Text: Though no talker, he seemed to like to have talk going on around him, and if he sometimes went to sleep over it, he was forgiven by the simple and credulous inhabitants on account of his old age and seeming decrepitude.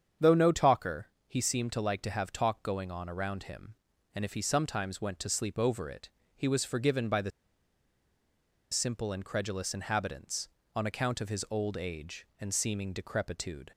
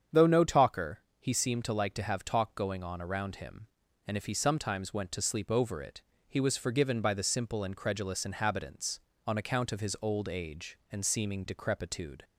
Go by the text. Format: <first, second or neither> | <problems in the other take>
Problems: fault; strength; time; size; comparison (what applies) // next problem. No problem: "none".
second | starts louder than the rest; strong; until 1.3 s; 8 dB; strong in the second // pauses between "the" and "simple"; strong; at 7.3 s; 1.4 s long